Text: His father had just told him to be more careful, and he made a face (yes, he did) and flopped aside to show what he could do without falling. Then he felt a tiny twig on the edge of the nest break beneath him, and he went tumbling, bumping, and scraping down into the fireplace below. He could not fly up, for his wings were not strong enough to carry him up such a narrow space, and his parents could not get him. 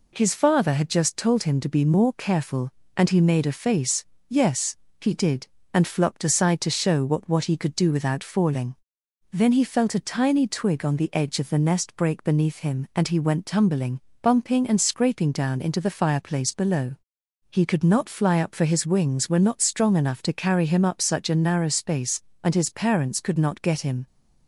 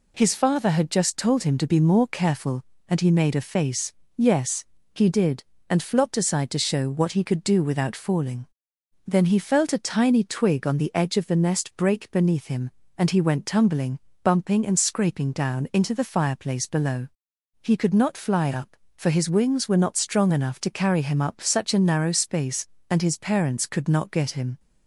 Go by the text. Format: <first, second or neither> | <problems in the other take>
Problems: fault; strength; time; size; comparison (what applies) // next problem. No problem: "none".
second | says "what" twice; at 7.2 s